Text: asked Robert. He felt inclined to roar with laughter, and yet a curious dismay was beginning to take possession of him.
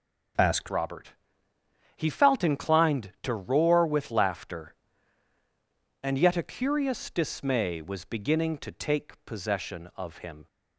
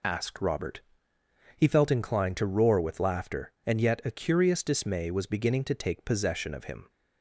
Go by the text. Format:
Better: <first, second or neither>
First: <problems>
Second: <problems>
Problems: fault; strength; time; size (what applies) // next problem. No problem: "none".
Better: second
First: changes voice at "Robert"; from 0.6 s on; 9.8 s long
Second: none